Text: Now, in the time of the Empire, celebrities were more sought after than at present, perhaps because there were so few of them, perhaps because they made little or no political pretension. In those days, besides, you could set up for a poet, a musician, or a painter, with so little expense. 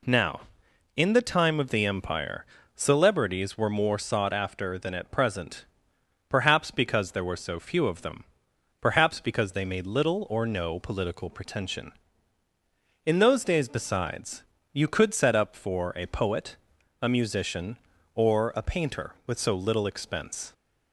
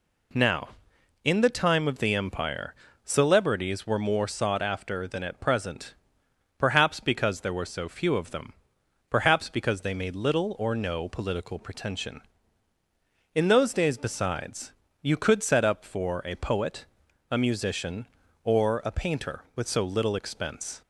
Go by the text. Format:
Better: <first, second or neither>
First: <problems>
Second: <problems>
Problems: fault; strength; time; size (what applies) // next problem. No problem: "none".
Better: neither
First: none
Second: none